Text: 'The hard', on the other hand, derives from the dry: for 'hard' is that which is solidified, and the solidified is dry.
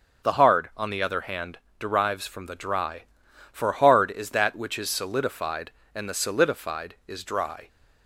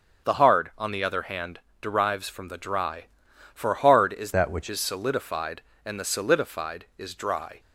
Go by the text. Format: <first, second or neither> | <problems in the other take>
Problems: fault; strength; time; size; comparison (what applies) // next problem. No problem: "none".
first | starts louder than the rest; until 1.3 s; 6.5 dB; also in the first // changes voice from "that" to "which"; from 4.3 to 4.6 s; 0.3 s long